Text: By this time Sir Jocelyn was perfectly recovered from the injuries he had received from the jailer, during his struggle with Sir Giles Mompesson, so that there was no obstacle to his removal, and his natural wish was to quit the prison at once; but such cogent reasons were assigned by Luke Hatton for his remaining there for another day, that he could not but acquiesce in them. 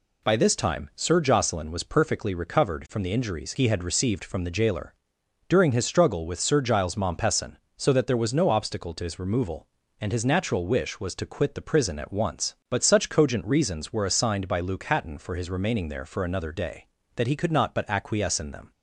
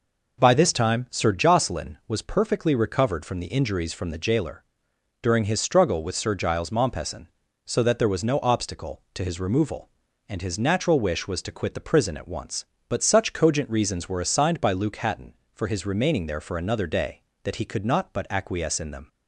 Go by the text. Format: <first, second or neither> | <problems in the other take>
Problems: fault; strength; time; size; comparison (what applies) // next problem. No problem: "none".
first | skips "he had received"; at 3.9 s